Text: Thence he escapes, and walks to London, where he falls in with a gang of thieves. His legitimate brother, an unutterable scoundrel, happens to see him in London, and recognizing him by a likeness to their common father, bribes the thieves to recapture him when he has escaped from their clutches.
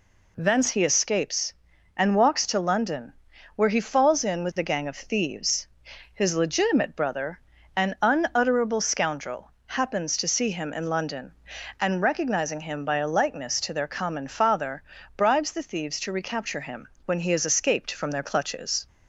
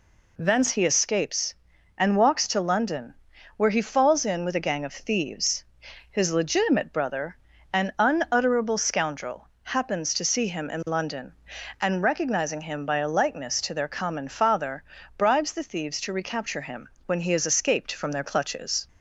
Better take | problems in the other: neither | pauses between "him" and "when"; slight; the same in both

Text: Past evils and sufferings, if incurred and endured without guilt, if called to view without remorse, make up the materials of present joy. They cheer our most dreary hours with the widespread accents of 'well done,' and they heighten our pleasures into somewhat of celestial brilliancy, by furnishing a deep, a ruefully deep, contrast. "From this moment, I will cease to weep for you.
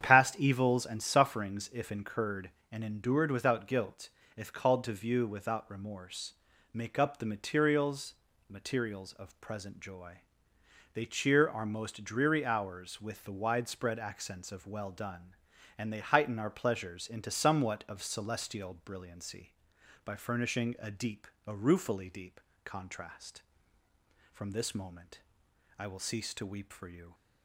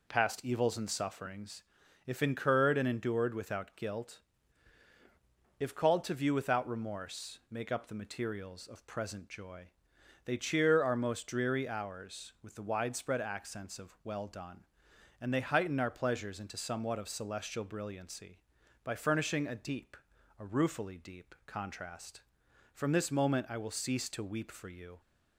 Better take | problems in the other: second | starts louder than the rest; strong; until 1.0 s; 8.5 dB // says "materials" twice; at 8.4 s

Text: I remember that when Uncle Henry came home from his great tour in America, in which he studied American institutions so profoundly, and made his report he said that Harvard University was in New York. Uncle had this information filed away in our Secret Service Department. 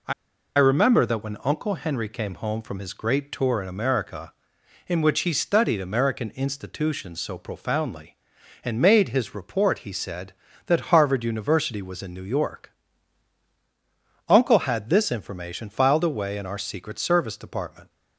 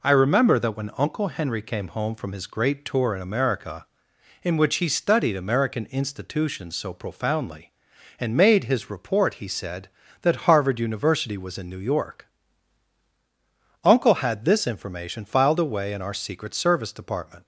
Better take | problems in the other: second | pauses between "I" and "remember"; at 0.1 s; 0.45 s long

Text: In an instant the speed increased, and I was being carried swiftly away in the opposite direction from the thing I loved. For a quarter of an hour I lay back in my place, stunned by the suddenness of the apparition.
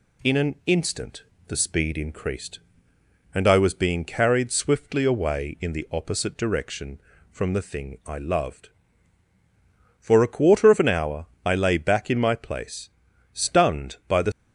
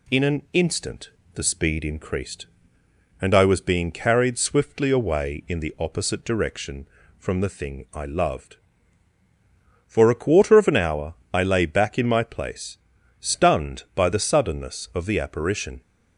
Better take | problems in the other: second | pauses between "instant" and "the"; slight; at 1.2 s; 0.24 s long; slight in the second // pauses between "hour" and "I"; slight; at 11.2 s; 0.18 s long; slight in the second // stops before "suddenness of the apparition"; at 14.3 s

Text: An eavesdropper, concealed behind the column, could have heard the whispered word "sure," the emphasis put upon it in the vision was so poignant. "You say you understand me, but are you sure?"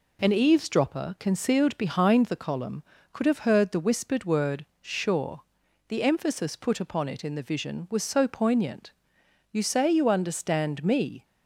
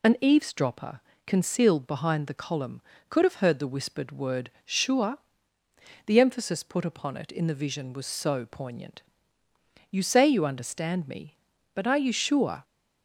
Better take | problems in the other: second | pauses between "word" and "sure"; slight; at 4.6 s; 0.16 s long // stops before "but are you sure"; at 11.2 s

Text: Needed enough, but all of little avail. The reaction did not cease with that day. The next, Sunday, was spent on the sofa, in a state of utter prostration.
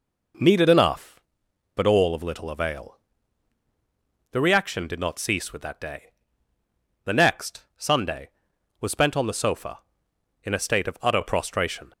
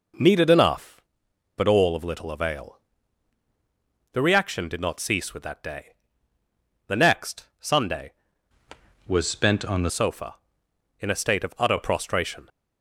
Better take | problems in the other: first | changes voice from "was" to "the"; from 9.0 to 9.9 s; 0.9 s long

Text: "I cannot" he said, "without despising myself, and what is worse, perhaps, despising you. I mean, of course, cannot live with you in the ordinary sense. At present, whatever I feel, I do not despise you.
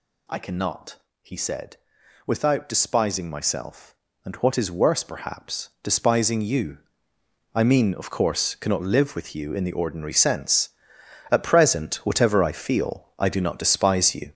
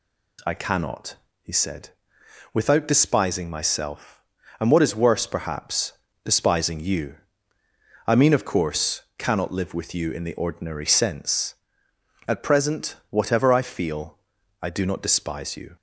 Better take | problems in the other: second | gets louder; throughout; 6 dB // pauses between "cannot" and "he"; slight; at 0.9 s; 0.26 s long; slight in the second

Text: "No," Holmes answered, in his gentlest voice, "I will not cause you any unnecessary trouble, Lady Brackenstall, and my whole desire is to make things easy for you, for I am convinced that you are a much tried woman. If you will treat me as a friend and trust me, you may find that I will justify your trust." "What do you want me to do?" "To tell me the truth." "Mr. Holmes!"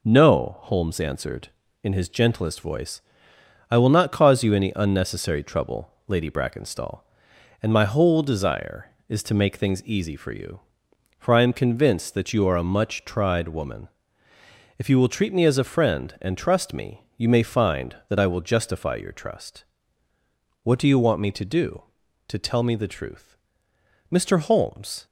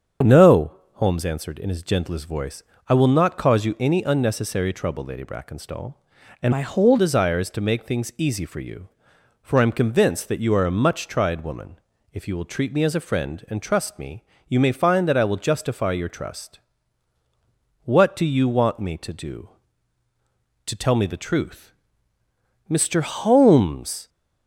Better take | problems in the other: first | starts louder than the rest; strong; until 1.4 s; 7.5 dB // changes voice from "my" to "whole"; from 6.5 to 6.9 s; 0.4 s long

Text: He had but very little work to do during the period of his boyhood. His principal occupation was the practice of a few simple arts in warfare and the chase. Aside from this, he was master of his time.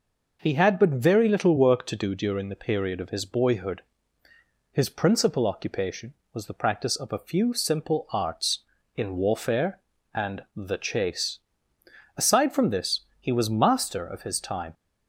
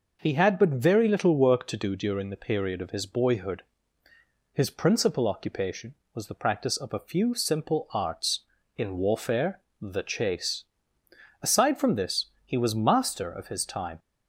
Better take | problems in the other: first | skips "and"; at 9.7 s

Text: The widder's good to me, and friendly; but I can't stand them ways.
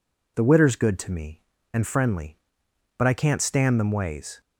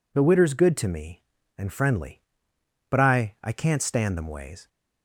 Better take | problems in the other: first | says "I" twice; at 3.4 s

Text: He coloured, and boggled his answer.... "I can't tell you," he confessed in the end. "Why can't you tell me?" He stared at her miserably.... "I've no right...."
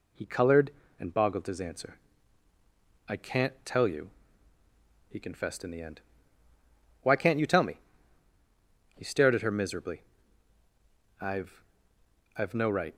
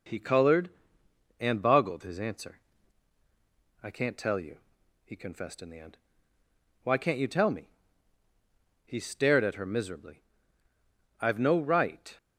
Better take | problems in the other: second | says "I've" twice; at 12.3 s

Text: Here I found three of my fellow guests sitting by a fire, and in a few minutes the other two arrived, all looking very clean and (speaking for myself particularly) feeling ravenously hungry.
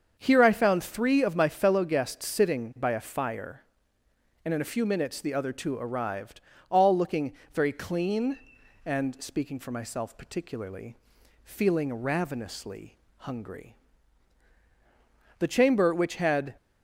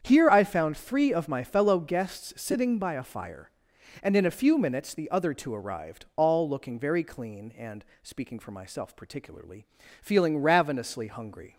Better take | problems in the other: second | starts louder than the rest; until 1.1 s; 7 dB; strong in the second // pauses between "looking" and "very"; slight; at 7.3 s; 0.20 s long // pauses between "ravenously" and "hungry"; slight; at 12.9 s; 0.20 s long // goes on to say "The chamber which had"; noticeable; from 15.3 s on; 1.1 s long

